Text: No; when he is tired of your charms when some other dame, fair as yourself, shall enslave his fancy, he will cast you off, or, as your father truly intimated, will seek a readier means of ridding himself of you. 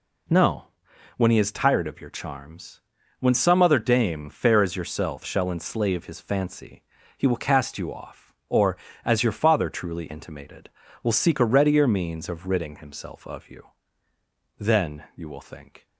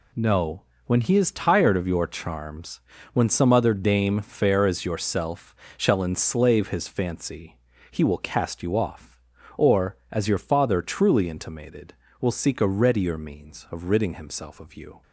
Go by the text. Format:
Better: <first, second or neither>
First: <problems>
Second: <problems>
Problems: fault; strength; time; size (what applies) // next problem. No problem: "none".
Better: second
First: pauses between "charms" and "when"; at 2.7 s; 0.40 s long // goes on to say "Then you will think"; noticeable; from 14.5 s on; 1.2 s long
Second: pauses between "charms" and "when"; slight; at 2.8 s; 0.34 s long